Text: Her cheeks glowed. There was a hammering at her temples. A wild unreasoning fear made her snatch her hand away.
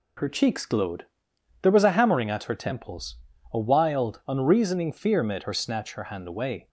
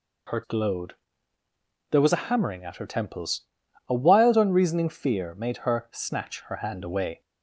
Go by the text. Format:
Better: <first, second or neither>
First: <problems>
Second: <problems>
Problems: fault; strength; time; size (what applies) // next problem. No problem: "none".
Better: first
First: none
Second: skips "cheeks"; at 0.4 s